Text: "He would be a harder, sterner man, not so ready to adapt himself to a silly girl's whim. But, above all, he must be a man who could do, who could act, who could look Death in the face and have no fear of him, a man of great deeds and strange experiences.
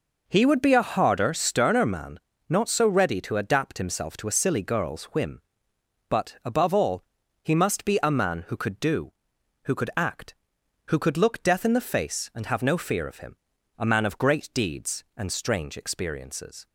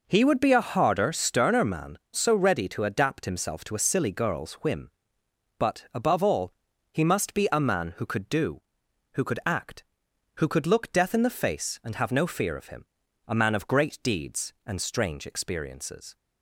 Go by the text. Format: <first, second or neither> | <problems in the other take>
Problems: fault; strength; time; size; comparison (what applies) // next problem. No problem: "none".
first | skips "not"; at 2.0 s